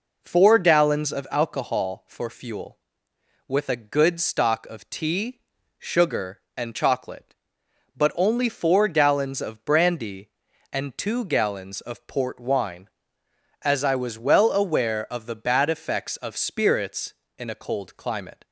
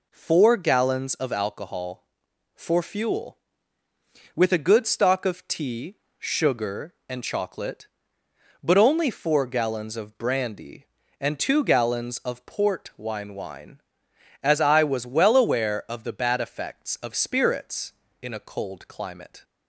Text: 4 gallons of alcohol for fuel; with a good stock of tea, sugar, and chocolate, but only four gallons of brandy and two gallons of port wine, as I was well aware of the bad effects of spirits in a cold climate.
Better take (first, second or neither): first